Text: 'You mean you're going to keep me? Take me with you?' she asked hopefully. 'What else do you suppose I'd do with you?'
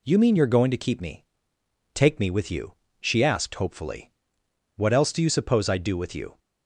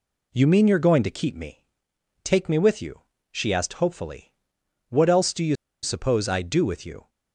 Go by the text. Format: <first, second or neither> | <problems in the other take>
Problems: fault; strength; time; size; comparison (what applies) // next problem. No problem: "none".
first | pauses between "you" and "suppose"; slight; at 5.5 s; 0.27 s long